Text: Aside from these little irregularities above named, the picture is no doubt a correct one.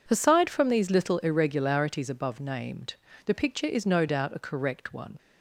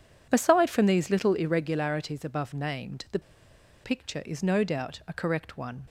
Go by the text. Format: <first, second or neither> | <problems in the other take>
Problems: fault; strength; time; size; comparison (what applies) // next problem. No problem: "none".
first | pauses between "the" and "picture"; noticeable; at 3.1 s; 0.63 s long